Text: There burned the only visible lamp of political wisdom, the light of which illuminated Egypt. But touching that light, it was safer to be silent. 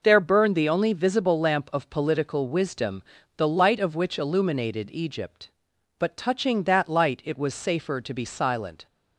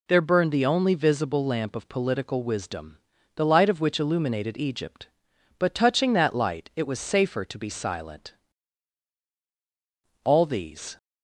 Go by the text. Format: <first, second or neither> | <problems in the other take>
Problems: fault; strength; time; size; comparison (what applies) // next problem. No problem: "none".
first | goes on to say "All these"; noticeable; from 10.2 s on; 0.72 s long